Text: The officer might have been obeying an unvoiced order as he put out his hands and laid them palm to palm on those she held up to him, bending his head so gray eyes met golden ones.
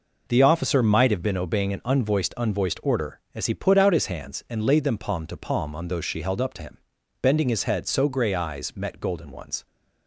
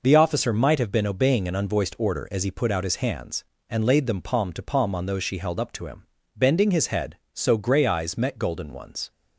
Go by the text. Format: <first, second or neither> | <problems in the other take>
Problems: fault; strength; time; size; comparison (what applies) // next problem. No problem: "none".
second | says "unvoiced" twice; at 2.3 s